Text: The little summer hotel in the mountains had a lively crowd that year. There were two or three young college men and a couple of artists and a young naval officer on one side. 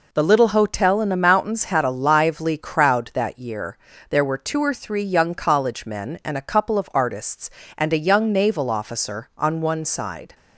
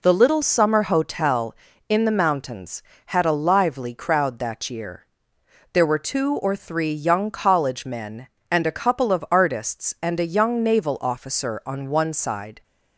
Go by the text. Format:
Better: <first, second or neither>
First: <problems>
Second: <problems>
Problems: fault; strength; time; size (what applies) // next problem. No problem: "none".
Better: second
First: skips "summer"; at 0.4 s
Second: none